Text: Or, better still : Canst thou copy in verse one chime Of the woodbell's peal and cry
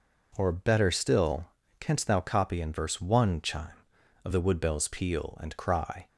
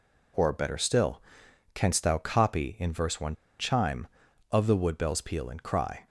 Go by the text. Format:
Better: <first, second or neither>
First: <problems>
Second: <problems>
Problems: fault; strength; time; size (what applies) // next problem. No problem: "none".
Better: first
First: none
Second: pauses between "one" and "chime"; slight; at 3.3 s; 0.24 s long